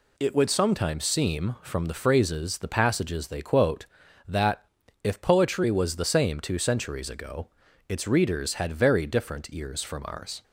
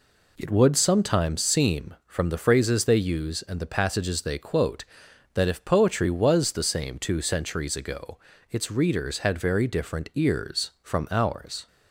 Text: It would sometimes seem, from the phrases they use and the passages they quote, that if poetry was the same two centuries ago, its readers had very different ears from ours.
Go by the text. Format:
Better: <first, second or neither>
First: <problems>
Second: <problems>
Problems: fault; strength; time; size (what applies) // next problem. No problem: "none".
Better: second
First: skips "they use and"; at 2.5 s // pauses between "that" and "if"; at 4.6 s; 0.38 s long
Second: none